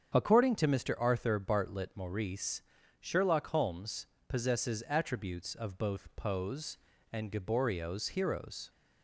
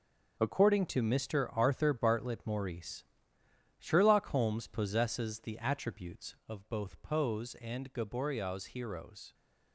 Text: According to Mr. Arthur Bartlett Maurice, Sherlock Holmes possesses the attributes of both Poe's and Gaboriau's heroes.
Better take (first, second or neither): second